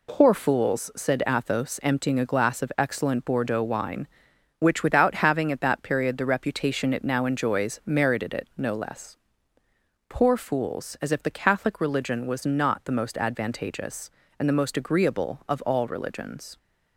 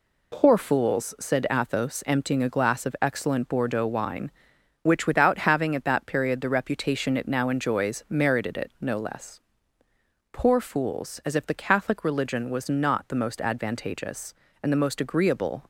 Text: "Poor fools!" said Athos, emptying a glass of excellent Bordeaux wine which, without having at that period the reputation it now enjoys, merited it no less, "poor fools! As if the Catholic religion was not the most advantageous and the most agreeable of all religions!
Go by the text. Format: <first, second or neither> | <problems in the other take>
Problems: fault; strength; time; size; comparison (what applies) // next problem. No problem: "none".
first | stops before "of all religions"; at 15.6 s